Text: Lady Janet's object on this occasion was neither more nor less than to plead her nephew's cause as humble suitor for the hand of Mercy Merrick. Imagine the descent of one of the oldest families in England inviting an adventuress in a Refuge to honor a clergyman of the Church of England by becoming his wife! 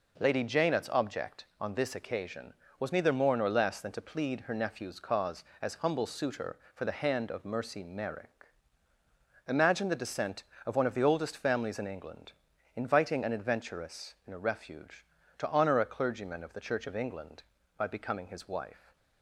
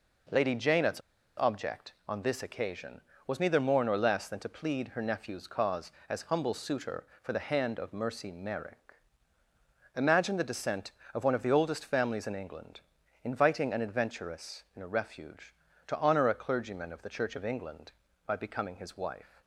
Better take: first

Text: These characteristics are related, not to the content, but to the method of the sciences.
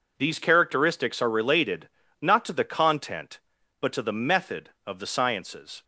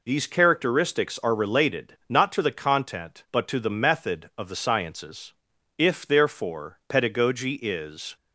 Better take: first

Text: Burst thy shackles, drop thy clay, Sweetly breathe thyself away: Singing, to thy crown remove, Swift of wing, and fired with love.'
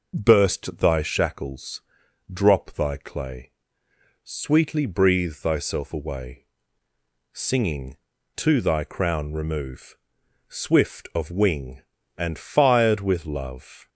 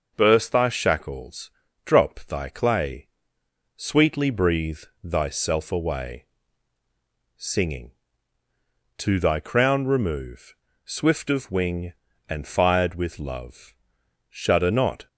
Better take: first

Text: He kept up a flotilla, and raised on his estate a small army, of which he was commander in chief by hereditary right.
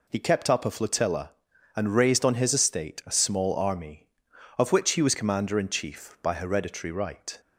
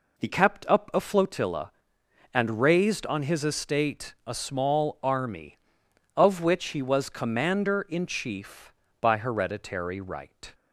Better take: first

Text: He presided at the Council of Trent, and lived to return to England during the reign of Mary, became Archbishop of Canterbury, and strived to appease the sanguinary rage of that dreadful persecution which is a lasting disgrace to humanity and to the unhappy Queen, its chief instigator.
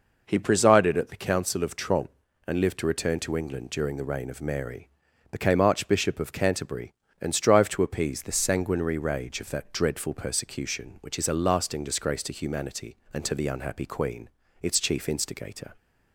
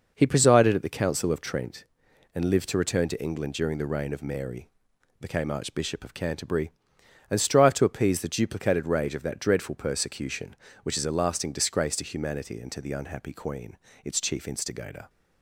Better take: first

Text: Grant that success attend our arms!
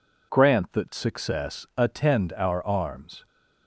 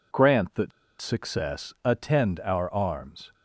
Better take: first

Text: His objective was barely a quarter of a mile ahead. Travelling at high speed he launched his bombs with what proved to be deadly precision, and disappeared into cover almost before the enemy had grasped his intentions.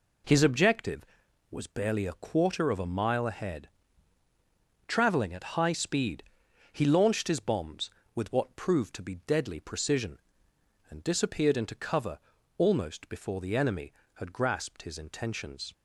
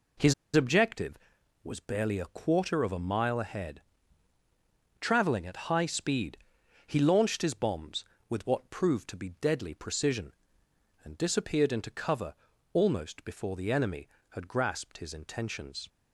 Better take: first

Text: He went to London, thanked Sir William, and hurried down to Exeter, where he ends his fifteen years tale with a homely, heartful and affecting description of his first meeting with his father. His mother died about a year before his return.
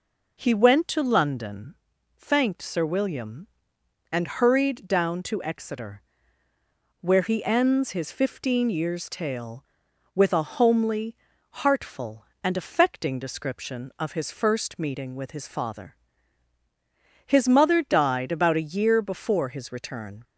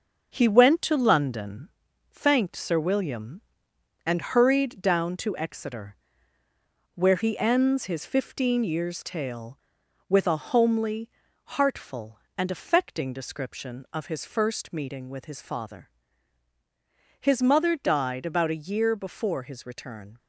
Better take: first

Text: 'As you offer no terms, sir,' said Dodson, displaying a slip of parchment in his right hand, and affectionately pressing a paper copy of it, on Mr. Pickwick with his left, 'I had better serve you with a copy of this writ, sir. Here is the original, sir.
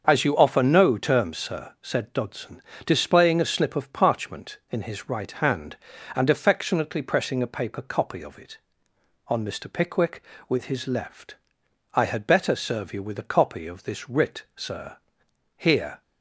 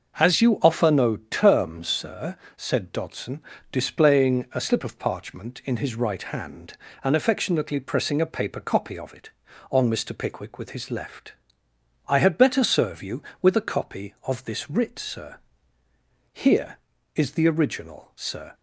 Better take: second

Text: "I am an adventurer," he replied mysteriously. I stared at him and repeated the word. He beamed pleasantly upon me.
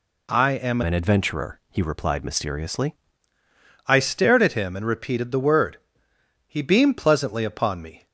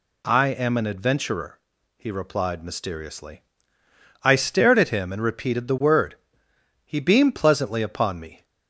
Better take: second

